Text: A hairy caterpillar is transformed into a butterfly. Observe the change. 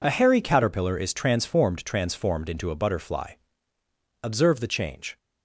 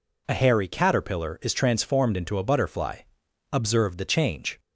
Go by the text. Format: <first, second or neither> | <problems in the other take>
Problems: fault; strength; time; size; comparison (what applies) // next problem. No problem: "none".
second | says "transformed" twice; at 1.8 s